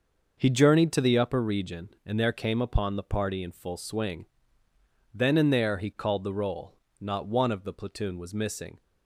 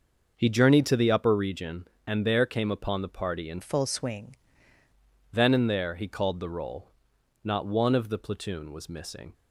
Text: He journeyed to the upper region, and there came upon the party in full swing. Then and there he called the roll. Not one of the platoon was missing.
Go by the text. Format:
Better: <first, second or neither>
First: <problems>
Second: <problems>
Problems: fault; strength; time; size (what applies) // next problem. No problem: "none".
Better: first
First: starts louder than the rest; noticeable; until 1.3 s; 6 dB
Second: starts louder than the rest; until 1.3 s; 6 dB // changes voice from "full" to "swing"; from 3.6 to 4.3 s; 0.7 s long